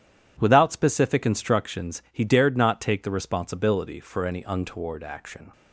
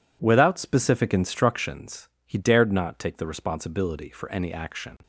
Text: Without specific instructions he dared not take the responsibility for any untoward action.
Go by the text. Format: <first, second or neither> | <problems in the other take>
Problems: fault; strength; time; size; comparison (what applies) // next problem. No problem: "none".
first | pauses between "instructions" and "he"; slight; at 2.0 s; 0.18 s long // skips "untoward"; at 4.5 s